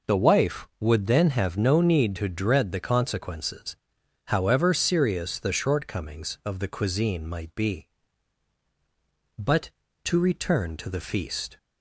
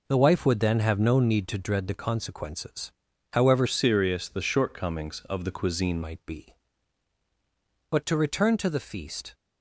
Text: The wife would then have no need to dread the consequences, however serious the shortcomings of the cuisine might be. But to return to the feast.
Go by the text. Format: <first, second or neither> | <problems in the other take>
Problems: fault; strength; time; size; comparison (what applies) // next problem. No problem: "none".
first | changes voice from "serious" to "cuisine"; from 3.6 to 6.0 s; 2.4 s long